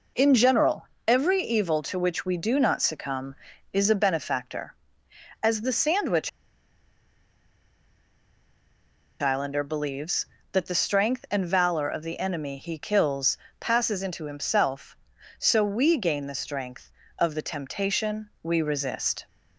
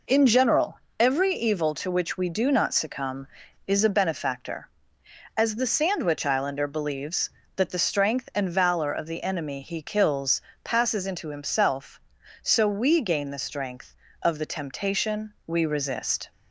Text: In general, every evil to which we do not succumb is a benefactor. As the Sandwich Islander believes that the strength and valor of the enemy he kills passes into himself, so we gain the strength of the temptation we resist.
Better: second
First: pauses between "Sandwich" and "Islander"; strong; at 6.2 s; 2.9 s long // pauses between "kills" and "passes"; slight; at 13.3 s; 0.22 s long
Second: pauses between "kills" and "passes"; slight; at 10.4 s; 0.22 s long

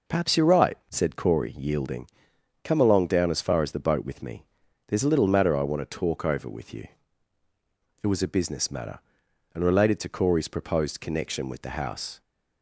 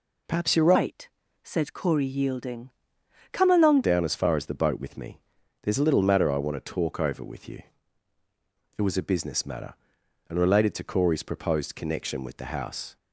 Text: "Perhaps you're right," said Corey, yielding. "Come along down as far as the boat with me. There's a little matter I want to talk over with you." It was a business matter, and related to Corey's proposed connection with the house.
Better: first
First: none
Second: changes voice from "right" to "along"; from 0.7 to 3.8 s; 3.1 s long

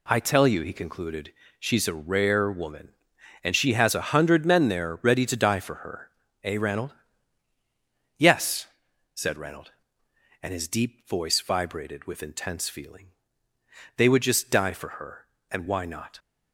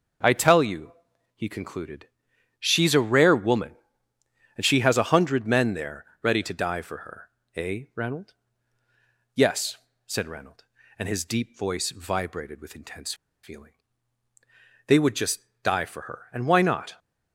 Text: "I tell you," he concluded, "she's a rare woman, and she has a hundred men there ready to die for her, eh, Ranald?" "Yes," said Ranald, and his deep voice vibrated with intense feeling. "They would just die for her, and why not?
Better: first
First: none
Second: pauses between "there" and "ready"; slight; at 6.0 s; 0.16 s long // pauses between "intense" and "feeling"; slight; at 13.1 s; 0.29 s long // pauses between "just" and "die"; slight; at 15.4 s; 0.22 s long

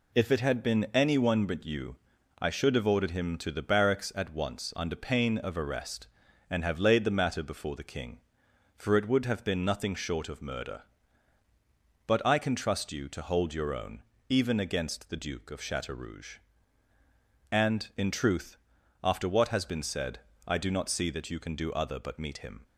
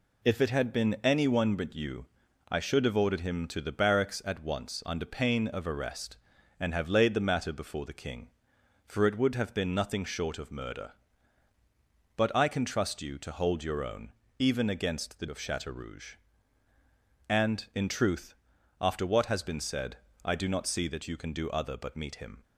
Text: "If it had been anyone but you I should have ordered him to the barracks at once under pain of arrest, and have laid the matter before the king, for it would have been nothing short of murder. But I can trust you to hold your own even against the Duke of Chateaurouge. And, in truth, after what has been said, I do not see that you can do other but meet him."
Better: first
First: pauses between "you" and "I"; at 1.9 s; 0.42 s long // pauses between "own" and "even"; slight; at 14.0 s; 0.26 s long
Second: pauses between "you" and "I"; at 2.0 s; 0.42 s long // pauses between "own" and "even"; slight; at 14.1 s; 0.26 s long // skips "Duke"; at 15.2 s

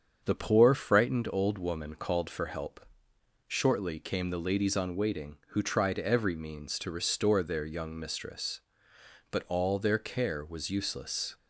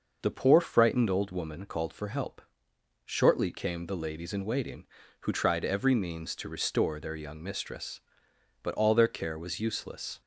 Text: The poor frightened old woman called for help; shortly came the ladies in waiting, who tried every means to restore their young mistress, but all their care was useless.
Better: second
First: starts louder than the rest; until 1.2 s; 7 dB // says "on" for "in"; at 4.7 s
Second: none

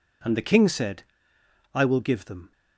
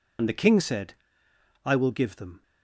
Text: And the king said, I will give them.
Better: first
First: none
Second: loses the start of "And"; at 0.1 s; 50 ms

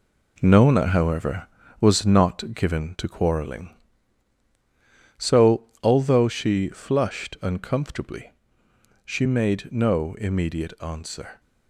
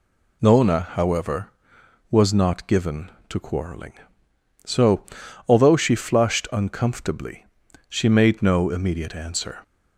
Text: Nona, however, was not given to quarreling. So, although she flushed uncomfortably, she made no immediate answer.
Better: second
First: gets quieter; throughout; 7 dB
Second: none

